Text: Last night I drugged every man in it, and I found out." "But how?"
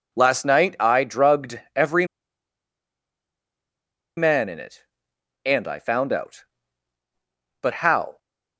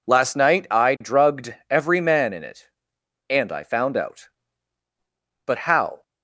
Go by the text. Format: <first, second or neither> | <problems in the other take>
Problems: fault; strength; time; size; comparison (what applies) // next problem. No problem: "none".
second | pauses between "drugged" and "every"; slight; at 1.5 s; 0.16 s long; slight in the second // pauses between "every" and "man"; strong; at 2.0 s; 2.1 s long